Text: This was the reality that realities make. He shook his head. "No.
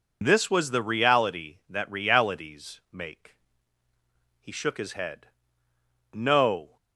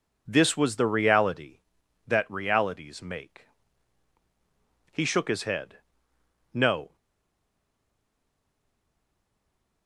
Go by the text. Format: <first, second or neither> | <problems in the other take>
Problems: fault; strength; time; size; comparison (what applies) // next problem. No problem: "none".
first | stays silent after the last word; strong; from 6.9 s on; 2.9 s long